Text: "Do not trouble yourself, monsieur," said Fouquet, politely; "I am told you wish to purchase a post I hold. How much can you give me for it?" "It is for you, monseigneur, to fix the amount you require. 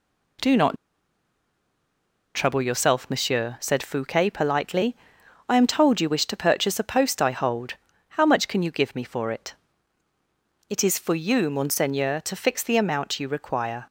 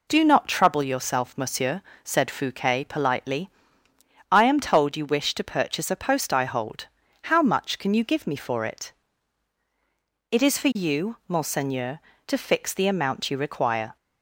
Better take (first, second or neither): second